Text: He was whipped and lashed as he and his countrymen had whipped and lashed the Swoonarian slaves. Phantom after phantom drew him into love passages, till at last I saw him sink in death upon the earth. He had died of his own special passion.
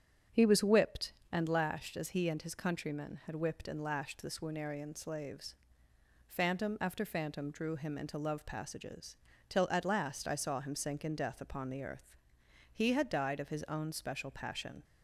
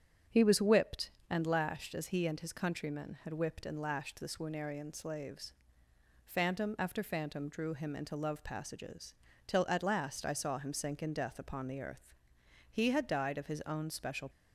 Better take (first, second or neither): first